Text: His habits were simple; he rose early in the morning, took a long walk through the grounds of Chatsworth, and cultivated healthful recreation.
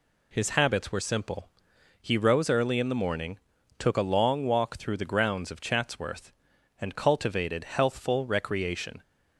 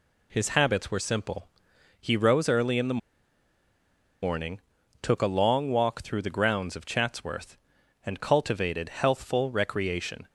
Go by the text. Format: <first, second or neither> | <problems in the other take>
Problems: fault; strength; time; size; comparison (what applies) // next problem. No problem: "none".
first | pauses between "the" and "morning"; at 2.9 s; 1.2 s long